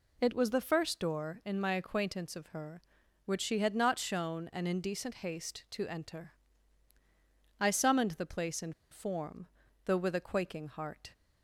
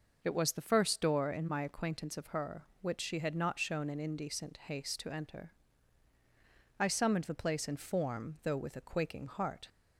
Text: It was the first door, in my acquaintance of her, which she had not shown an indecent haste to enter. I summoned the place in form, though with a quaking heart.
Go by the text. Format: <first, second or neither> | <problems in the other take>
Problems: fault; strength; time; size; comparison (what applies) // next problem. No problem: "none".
second | pauses between "in" and "form"; slight; at 8.7 s; 0.18 s long